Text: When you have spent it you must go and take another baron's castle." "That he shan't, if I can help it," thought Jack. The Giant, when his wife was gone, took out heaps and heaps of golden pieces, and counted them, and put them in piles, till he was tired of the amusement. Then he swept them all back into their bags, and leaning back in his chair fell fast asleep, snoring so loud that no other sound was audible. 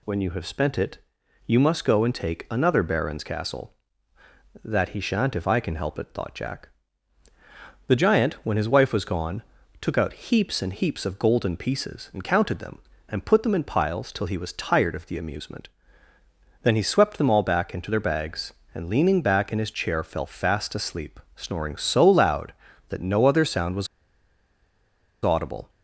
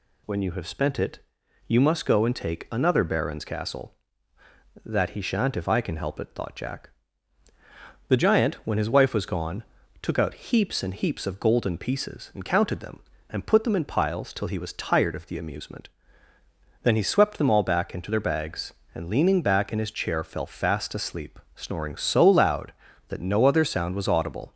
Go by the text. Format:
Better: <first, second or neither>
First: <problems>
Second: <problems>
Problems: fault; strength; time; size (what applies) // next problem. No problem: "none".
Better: second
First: pauses between "it" and "you"; noticeable; at 0.9 s; 0.48 s long // pauses between "was" and "audible"; strong; at 23.8 s; 1.3 s long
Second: pauses between "it" and "you"; noticeable; at 1.1 s; 0.48 s long